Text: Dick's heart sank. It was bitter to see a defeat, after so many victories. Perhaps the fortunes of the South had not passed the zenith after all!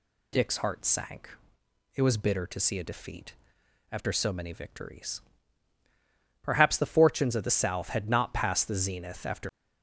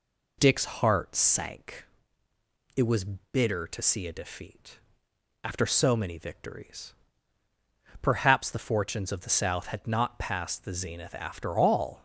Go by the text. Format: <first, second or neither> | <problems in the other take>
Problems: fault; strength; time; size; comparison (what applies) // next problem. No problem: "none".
second | stops before "all"; at 9.5 s